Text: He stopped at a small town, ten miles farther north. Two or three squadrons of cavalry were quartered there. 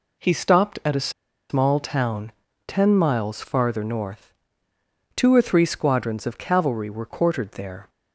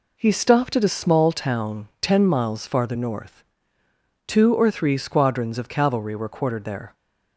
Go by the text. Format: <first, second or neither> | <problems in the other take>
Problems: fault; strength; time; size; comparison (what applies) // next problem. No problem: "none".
second | pauses between "a" and "small"; at 1.0 s; 0.40 s long